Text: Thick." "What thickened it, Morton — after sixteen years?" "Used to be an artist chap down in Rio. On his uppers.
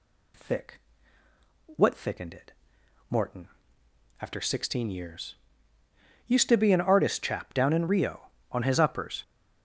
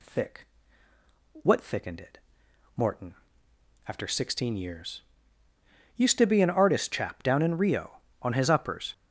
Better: neither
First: none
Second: none

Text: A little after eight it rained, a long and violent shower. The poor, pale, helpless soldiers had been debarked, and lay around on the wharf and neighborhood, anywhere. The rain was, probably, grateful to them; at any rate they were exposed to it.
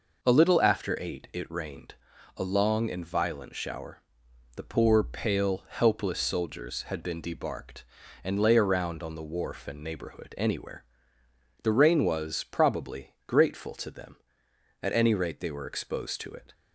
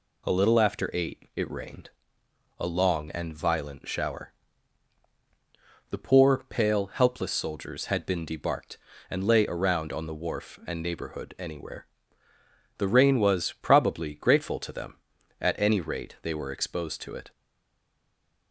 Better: first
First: none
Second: stays silent after the last word; noticeable; from 17.3 s on; 1.2 s long

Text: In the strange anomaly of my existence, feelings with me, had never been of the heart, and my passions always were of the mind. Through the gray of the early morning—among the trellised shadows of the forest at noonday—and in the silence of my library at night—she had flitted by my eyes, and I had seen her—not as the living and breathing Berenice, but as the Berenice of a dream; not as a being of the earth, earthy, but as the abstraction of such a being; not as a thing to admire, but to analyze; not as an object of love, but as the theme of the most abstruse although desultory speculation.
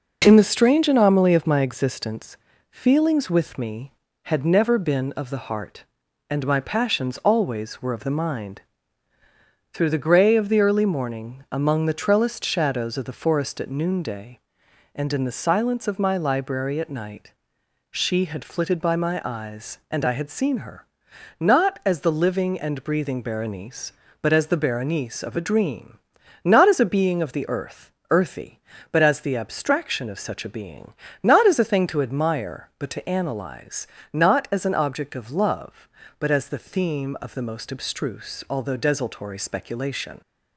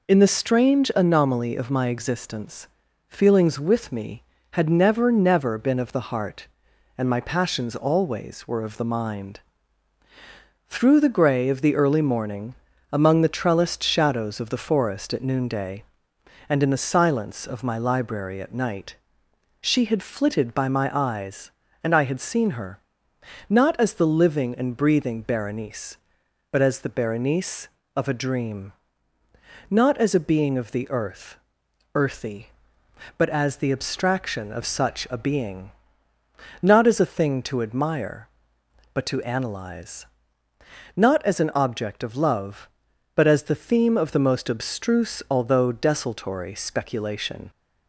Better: first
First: none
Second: says "never" twice; at 5.1 s

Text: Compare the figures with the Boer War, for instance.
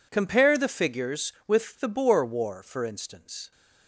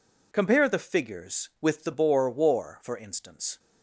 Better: neither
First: none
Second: none

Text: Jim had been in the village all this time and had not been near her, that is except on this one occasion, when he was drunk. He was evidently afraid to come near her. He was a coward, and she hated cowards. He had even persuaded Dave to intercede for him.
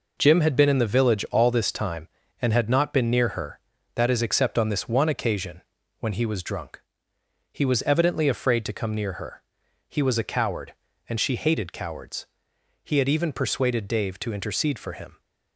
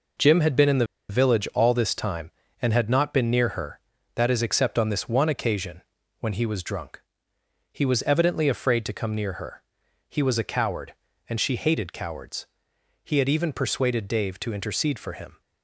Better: first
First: none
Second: pauses between "the" and "village"; slight; at 0.8 s; 0.23 s long

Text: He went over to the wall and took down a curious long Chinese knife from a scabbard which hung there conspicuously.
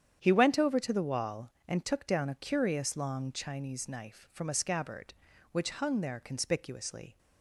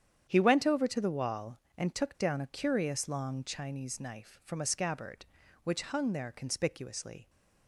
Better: neither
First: starts louder than the rest; strong; until 1.2 s; 9 dB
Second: starts louder than the rest; strong; until 1.3 s; 9 dB

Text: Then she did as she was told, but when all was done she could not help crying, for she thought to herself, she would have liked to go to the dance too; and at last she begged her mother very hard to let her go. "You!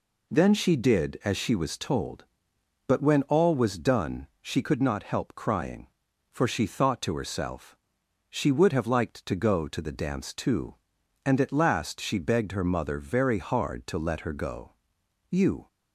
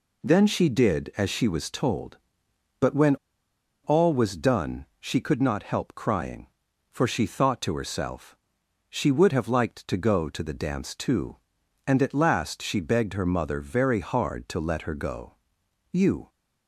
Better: first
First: pauses between "done" and "she"; slight; at 4.2 s; 0.16 s long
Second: pauses between "when" and "all"; noticeable; at 3.1 s; 0.68 s long // pauses between "done" and "she"; slight; at 4.8 s; 0.16 s long

